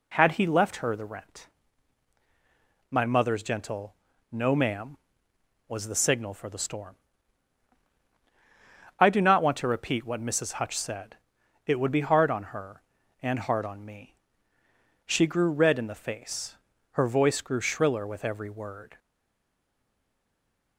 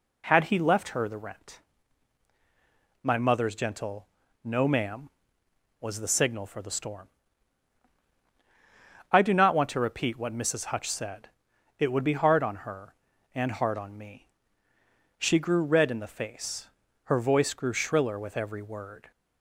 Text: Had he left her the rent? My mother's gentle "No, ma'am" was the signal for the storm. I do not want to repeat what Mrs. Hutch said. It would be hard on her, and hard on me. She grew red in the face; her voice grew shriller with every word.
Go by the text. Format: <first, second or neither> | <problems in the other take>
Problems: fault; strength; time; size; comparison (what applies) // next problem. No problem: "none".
second | pauses between "gentle" and "No"; slight; at 3.9 s; 0.36 s long; slight in the second // stays silent after the last word; noticeable; from 18.9 s on; 1.8 s long